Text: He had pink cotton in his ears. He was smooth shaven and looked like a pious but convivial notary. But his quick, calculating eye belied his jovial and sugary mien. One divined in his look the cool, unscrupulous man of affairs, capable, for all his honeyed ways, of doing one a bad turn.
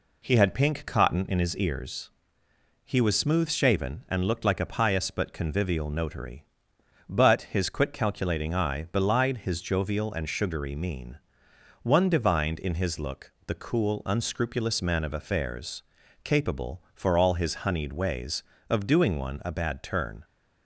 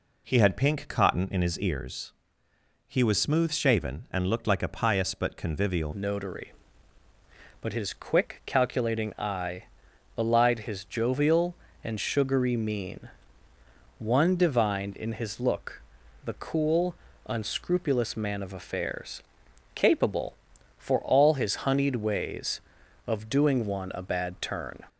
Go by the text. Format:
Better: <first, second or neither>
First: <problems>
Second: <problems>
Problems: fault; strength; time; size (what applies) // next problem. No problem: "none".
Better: first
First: pauses between "look" and "the"; slight; at 13.3 s; 0.16 s long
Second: changes voice at "notary"; from 5.9 s on; 18.9 s long // pauses between "eye" and "belied"; noticeable; at 9.6 s; 0.54 s long // pauses between "look" and "the"; at 15.8 s; 0.44 s long